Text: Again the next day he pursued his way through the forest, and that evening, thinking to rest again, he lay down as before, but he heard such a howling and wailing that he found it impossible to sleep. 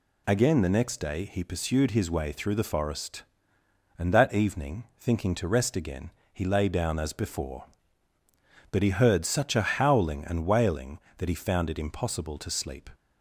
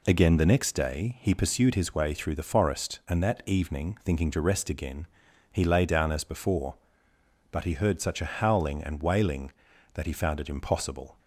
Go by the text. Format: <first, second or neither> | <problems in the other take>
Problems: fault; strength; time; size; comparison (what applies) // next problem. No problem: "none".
first | stops before "to sleep"; at 11.1 s